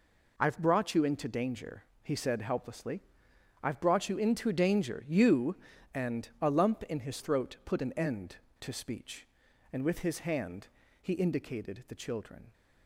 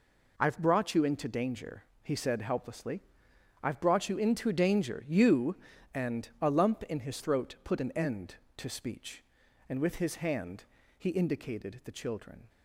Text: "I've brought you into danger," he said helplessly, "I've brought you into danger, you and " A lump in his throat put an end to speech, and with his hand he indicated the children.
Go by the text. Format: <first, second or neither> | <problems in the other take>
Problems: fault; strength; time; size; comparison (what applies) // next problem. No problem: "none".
neither | pauses between "hand" and "he"; slight; the same in both